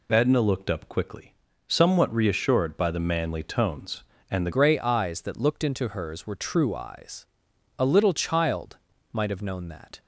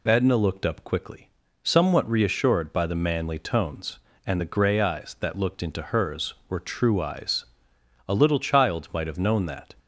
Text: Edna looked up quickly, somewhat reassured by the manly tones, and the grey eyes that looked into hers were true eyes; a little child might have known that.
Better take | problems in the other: second | changes voice at "grey"; from 4.5 s on; 5.5 s long // pauses between "child" and "might"; slight; at 8.7 s; 0.34 s long

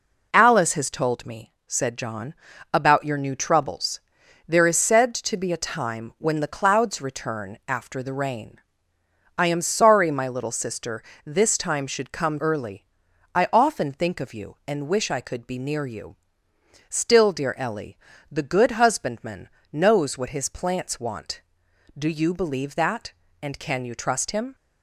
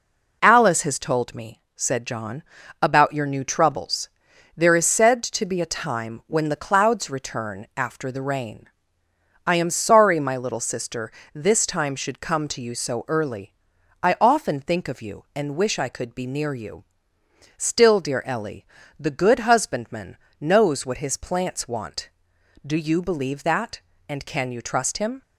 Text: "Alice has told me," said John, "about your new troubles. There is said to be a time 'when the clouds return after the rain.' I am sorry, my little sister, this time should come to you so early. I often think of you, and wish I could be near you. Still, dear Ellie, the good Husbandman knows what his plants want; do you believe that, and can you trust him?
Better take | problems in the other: second | skips "to you so"; at 12.3 s // pauses between "Husbandman" and "knows"; slight; at 19.4 s; 0.22 s long; slight in the second

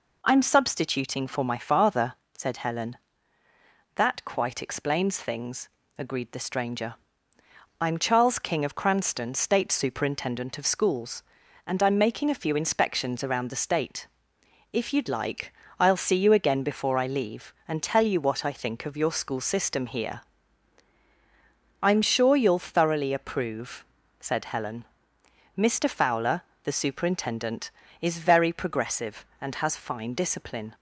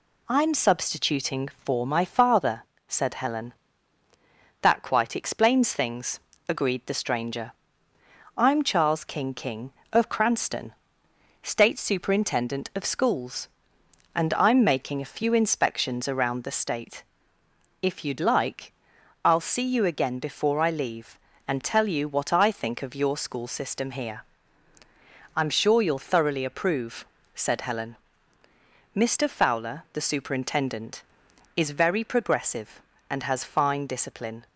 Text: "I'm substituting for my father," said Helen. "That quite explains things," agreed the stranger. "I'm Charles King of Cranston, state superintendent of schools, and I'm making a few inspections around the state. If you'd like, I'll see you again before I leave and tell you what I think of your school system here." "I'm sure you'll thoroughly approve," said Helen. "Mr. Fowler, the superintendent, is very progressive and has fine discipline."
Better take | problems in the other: first | says "King" twice; at 9.3 s

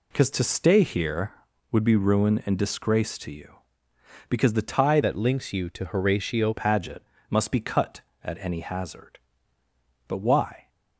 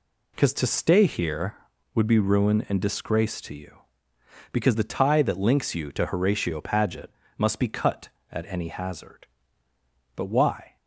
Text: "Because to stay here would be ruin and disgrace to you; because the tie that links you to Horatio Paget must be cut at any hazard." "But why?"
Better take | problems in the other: second | changes voice from "that" to "Horatio"; from 5.0 to 6.5 s; 1.5 s long // pauses between "Paget" and "must"; slight; at 7.0 s; 0.26 s long; slight in the second

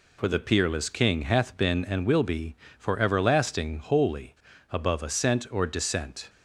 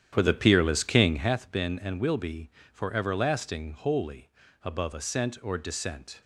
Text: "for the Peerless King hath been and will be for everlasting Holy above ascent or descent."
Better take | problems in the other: first | starts louder than the rest; strong; until 1.3 s; 10 dB // pauses between "Holy" and "above"; slight; at 4.2 s; 0.32 s long; slight in the first

